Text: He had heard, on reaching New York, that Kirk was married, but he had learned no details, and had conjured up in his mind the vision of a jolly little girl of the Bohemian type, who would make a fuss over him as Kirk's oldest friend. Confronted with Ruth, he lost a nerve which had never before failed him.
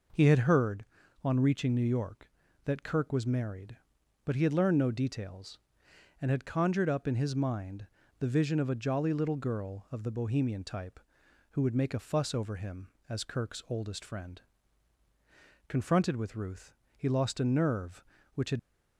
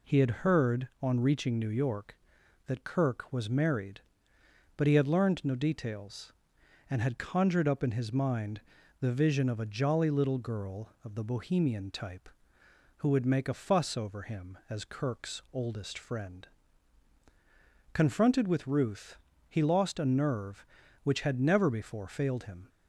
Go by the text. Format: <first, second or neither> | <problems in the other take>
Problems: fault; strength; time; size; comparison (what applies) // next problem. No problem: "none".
second | pauses between "mind" and "the"; slight; at 7.8 s; 0.32 s long; also in the second // stops before "never before failed him"; at 18.5 s